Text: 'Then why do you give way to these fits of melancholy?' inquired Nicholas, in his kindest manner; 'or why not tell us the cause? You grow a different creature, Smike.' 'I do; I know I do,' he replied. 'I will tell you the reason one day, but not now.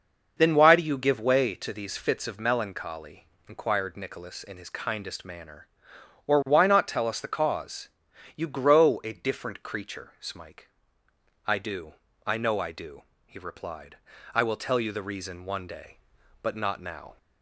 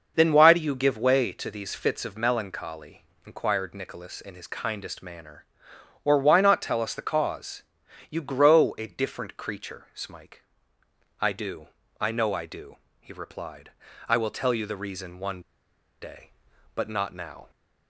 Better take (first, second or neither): first